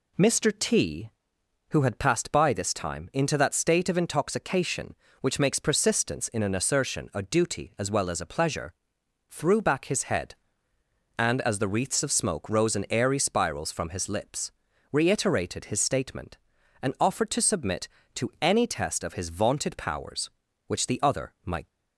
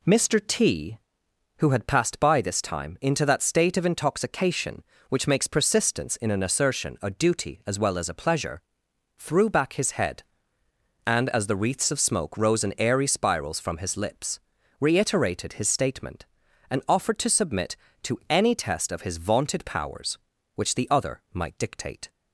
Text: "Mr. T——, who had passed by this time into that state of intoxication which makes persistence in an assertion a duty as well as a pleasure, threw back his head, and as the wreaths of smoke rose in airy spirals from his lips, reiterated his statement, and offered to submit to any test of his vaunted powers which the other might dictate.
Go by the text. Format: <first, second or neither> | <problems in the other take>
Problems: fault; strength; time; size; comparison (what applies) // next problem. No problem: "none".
second | stops before "dictate"; at 21.6 s